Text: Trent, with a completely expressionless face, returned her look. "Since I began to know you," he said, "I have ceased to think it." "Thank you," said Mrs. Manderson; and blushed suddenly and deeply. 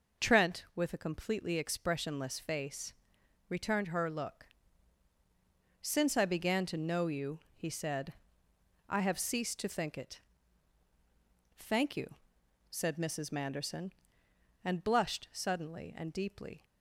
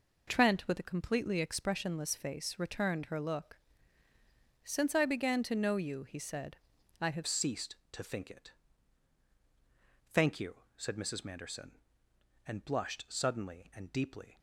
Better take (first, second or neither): first